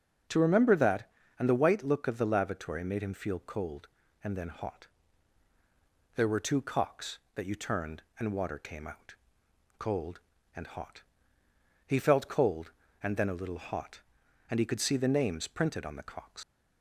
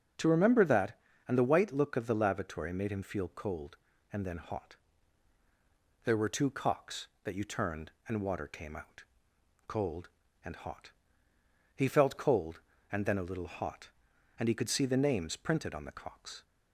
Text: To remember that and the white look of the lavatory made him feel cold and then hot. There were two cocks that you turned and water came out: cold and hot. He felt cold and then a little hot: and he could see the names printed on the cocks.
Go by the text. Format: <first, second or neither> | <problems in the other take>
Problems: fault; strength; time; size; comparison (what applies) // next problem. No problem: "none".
second | starts louder than the rest; until 1.5 s; 6.5 dB; also in the second // leaves "cocks" unfinished; at 16.4 s; 115 ms